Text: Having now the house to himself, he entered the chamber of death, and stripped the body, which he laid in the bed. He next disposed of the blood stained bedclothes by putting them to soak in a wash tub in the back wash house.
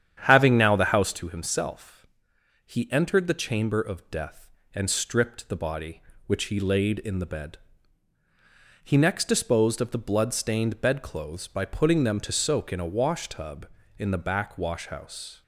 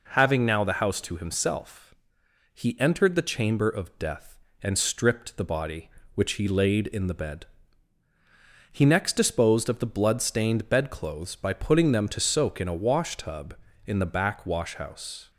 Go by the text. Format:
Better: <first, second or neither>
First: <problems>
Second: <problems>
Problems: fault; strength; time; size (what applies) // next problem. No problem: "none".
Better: second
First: starts louder than the rest; strong; until 1.2 s; 9 dB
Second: none